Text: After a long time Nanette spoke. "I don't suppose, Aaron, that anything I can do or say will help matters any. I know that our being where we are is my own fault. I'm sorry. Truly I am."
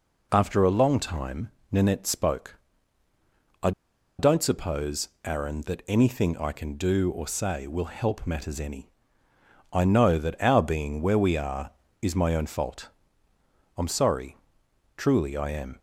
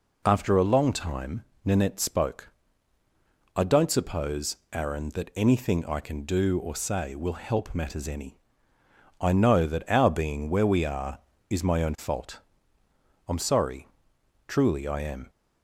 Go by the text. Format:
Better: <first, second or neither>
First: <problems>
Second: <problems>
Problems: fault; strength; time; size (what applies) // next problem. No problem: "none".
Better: second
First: pauses between "time" and "Nanette"; slight; at 1.4 s; 0.22 s long // pauses between "I" and "don't"; noticeable; at 3.7 s; 0.47 s long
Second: pauses between "time" and "Nanette"; slight; at 1.4 s; 0.22 s long